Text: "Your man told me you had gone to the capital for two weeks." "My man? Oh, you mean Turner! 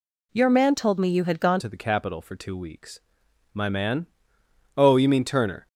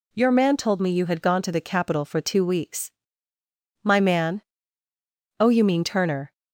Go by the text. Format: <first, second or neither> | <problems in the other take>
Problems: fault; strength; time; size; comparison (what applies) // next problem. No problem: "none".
second | changes voice at "to"; from 1.5 s on; 4.1 s long